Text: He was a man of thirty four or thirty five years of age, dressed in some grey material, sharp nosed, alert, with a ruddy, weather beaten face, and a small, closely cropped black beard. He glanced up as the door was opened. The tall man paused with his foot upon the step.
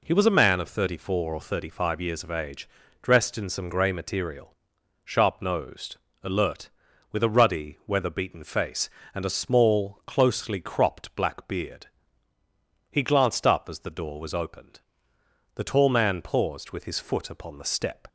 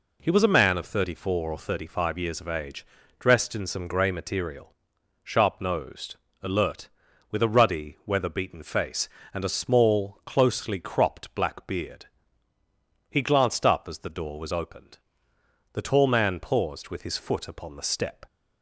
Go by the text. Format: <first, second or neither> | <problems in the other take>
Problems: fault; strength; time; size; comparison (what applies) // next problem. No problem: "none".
neither | none